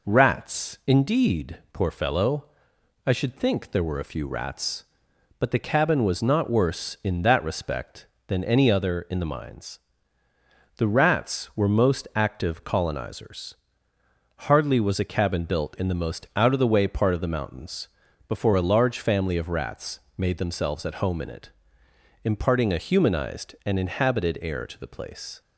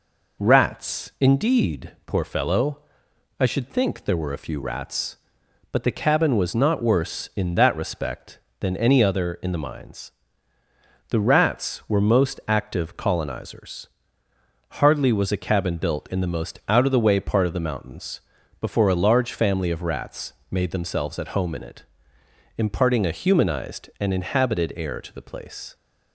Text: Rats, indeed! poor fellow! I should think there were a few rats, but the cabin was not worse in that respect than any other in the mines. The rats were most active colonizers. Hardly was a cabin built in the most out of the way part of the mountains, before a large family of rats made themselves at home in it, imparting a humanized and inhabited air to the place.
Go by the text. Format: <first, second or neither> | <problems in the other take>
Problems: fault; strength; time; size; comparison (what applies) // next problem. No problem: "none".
neither | pauses between "rats" and "made"; slight; the same in both